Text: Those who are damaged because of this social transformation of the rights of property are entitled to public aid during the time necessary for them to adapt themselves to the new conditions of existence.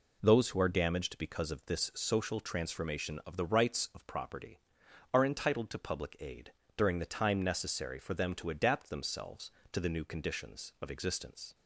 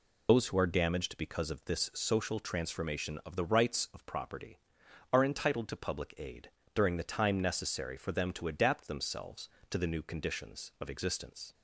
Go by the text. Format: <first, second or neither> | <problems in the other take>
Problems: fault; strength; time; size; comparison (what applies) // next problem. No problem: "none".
first | loses the start of "Those"; at 0.2 s; 115 ms // pauses between "aid" and "during"; slight; at 6.4 s; 0.24 s long; slight in the first